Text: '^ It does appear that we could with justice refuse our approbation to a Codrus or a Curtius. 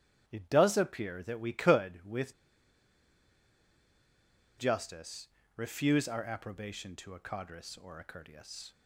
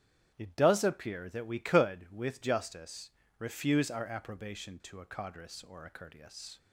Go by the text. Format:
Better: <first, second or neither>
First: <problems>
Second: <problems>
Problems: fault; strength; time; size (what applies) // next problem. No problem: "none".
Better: second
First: starts louder than the rest; strong; until 1.2 s; 9.5 dB // pauses between "with" and "justice"; strong; at 2.3 s; 2.2 s long // pauses between "justice" and "refuse"; slight; at 5.2 s; 0.28 s long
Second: starts louder than the rest; strong; until 1.3 s; 9.5 dB // pauses between "justice" and "refuse"; slight; at 3.0 s; 0.28 s long